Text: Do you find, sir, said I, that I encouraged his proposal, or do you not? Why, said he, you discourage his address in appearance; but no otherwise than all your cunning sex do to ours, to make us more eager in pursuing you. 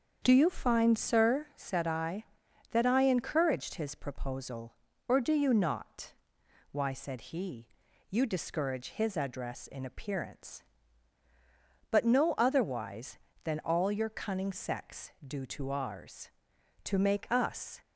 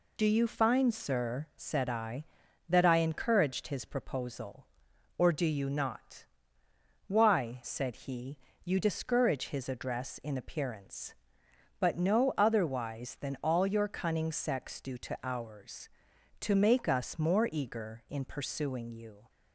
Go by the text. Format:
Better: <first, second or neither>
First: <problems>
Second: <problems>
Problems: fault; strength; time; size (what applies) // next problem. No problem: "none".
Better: second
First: starts louder than the rest; until 1.2 s; 7 dB // stops before "more eager in pursuing you"; at 17.8 s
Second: none